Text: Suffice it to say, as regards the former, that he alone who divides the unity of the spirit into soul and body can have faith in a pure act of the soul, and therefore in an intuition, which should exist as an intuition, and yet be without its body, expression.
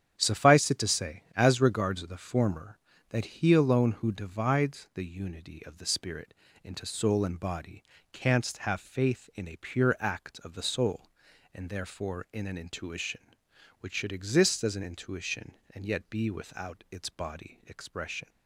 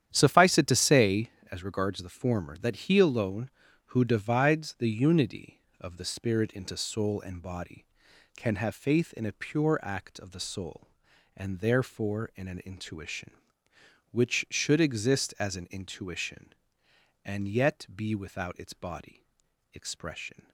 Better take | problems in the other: second | starts louder than the rest; strong; until 1.1 s; 9 dB; strong in the second // pauses between "spirit" and "into"; slight; at 6.3 s; 0.30 s long // says "canst" for "can"; at 8.1 s

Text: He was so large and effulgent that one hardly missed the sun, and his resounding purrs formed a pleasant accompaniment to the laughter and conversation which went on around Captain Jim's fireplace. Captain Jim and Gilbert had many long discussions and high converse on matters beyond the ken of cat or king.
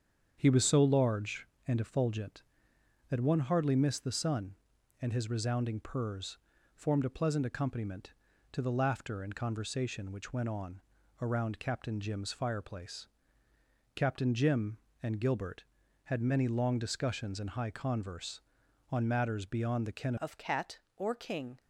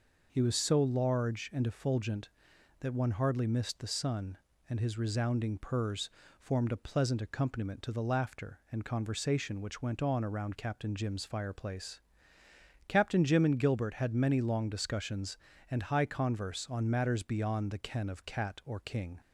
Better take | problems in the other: second | starts louder than the rest; strong; until 1.3 s; 7.5 dB // pauses between "purrs" and "formed"; at 6.3 s; 0.40 s long; slight in the second // pauses between "on" and "around"; at 10.8 s; 0.40 s long // changes voice at "of"; from 20.1 s on; 1.4 s long

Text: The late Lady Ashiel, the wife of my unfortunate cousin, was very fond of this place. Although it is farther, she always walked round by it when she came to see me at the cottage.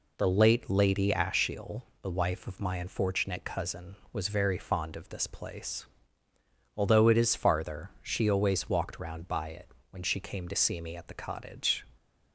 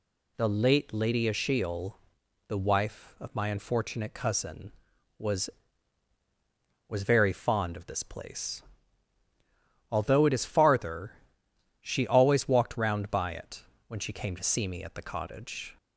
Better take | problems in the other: first | says "was" twice; at 6.8 s // pauses between "it" and "when"; slight; at 13.6 s; 0.24 s long; slight in the first

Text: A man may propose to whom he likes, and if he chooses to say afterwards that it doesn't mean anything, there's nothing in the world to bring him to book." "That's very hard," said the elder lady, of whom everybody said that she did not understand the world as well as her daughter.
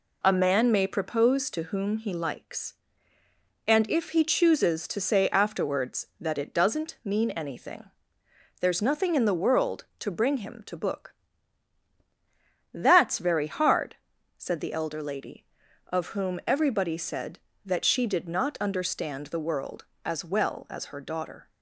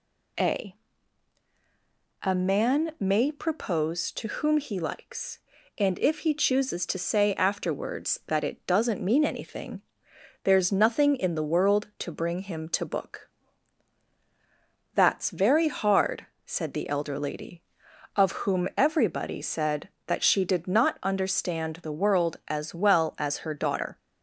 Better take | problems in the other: first | says "A" twice; at 2.2 s

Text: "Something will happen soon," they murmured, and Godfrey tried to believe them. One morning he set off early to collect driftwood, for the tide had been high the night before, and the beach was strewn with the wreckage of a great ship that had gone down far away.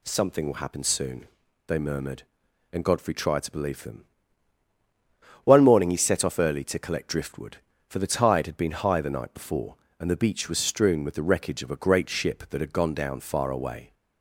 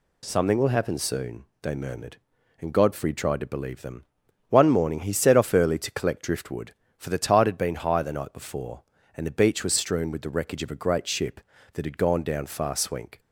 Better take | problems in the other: first | says "swink" for "away"; at 12.7 s

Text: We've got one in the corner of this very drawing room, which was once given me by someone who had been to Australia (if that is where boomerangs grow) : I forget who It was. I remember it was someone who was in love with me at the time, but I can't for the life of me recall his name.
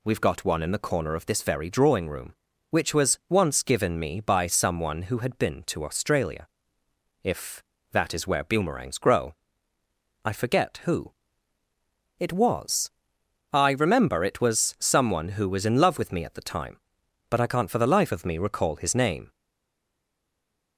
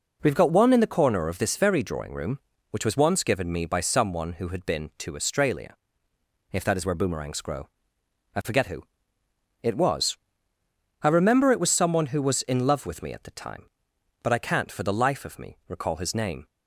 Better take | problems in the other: second | pauses between "who" and "It"; at 11.1 s; 1.0 s long; noticeable in the second // stays silent after the last word; noticeable; from 19.3 s on; 1.4 s long

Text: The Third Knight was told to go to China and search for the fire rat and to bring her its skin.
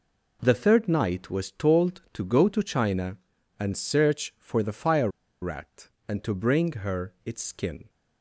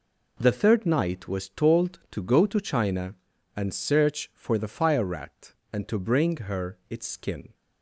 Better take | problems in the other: second | pauses between "fire" and "rat"; slight; at 5.0 s; 0.33 s long

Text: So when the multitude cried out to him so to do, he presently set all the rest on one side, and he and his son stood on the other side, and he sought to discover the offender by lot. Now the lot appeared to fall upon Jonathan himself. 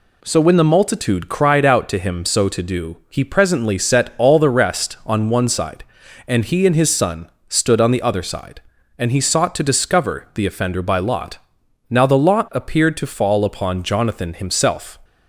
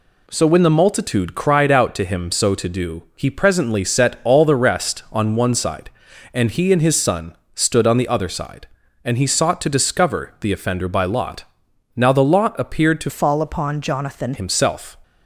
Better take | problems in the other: first | pauses between "son" and "stood"; slight; at 7.3 s; 0.18 s long; slight in the first // changes voice from "fall" to "Jonathan"; from 13.0 to 14.3 s; 1.3 s long

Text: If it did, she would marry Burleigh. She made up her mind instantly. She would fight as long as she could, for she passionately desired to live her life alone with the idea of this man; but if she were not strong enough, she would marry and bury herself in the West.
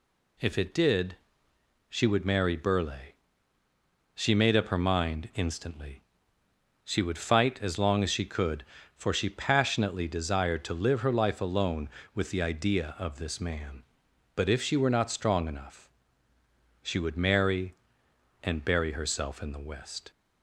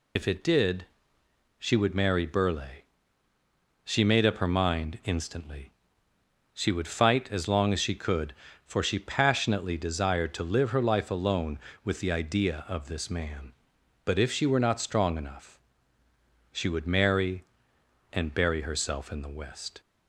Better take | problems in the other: first | loses the start of "If"; at 0.1 s; 65 ms

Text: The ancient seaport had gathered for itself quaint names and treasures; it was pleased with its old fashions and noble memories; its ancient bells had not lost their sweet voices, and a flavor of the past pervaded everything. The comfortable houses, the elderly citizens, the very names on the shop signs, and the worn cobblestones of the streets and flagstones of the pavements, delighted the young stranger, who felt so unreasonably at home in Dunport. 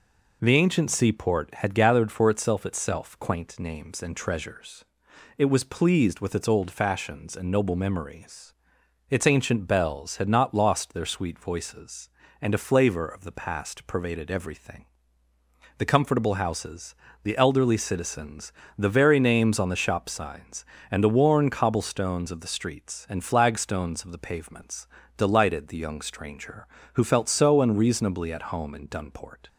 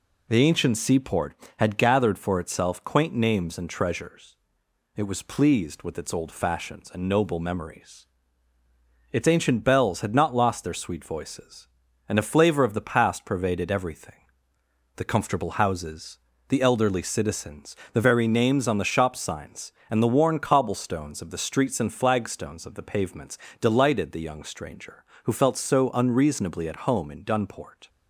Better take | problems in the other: second | says "itself" twice; at 2.6 s

